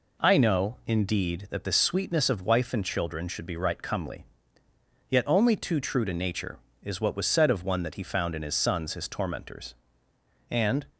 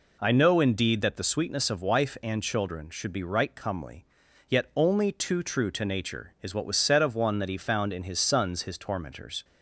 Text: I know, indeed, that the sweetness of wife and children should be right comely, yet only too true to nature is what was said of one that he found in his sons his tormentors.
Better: second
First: goes on to say "And"; slight; from 10.4 s on; 0.36 s long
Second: none

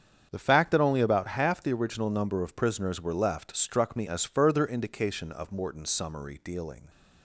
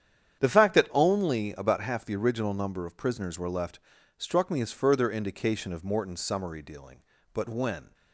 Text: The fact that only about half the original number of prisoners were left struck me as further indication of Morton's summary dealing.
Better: first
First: starts louder than the rest; strong; until 1.3 s; 8 dB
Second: starts louder than the rest; strong; until 1.4 s; 9 dB // pauses between "left" and "struck"; at 3.7 s; 0.40 s long // goes on to say "But when"; from 7.3 s on; 0.60 s long

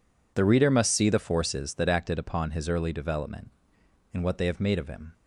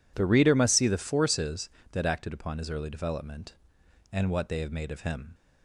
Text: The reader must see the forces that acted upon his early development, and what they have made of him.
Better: neither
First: none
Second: none

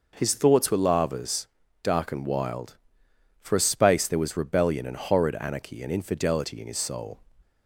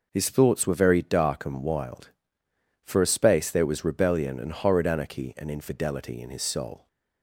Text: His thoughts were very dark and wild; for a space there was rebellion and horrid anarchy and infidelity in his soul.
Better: second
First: says "lavas" for "very"; at 0.7 s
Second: none

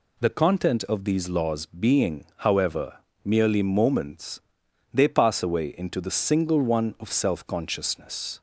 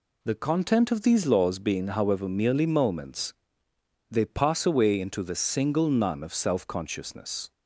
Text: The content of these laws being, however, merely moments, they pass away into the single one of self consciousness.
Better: first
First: none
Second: says "none" for "one"; at 5.8 s

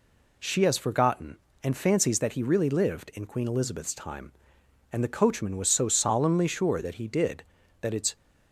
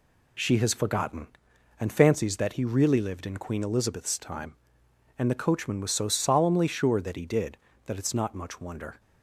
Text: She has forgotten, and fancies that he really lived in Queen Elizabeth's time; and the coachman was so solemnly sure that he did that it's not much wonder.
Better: second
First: stops before "not much wonder"; at 8.1 s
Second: none

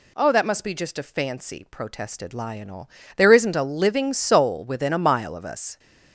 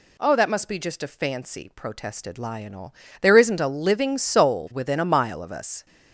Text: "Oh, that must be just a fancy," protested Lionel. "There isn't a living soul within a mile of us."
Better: neither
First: none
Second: none

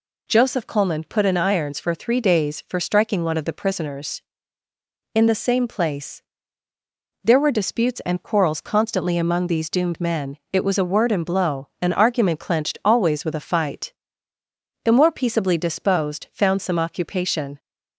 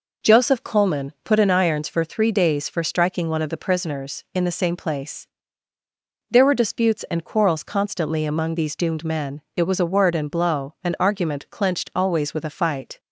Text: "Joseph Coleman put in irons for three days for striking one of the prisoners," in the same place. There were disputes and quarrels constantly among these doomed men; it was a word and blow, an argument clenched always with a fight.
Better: second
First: goes on to say "The more peaceably disposed found some occupation"; strong; from 14.8 s on; 2.7 s long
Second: none

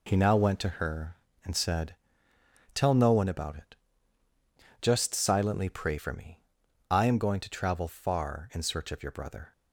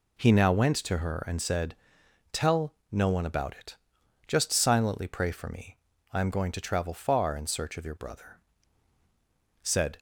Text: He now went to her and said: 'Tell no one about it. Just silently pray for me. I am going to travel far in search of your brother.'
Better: first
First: none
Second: pauses between "Tell" and "no"; slight; at 2.7 s; 0.18 s long // goes on to say "Said"; slight; from 9.6 s on; 0.36 s long

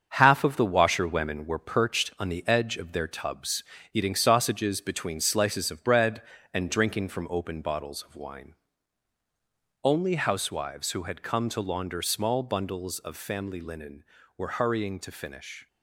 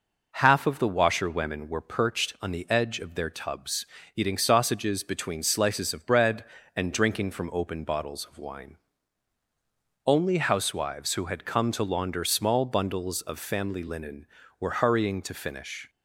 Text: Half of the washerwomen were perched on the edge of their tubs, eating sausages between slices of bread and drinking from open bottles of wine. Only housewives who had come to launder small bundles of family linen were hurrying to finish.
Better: second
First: gets quieter; throughout; 6.5 dB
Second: none

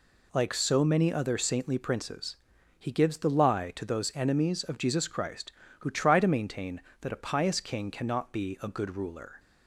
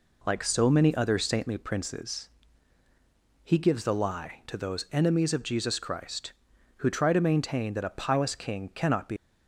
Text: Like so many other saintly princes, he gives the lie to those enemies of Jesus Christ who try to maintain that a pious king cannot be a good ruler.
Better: first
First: none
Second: stops before "a good ruler"; at 9.1 s

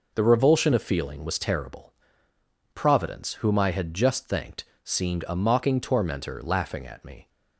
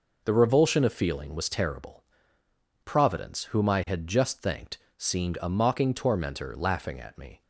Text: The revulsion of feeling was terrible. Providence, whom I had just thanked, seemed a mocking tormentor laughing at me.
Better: neither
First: none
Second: none

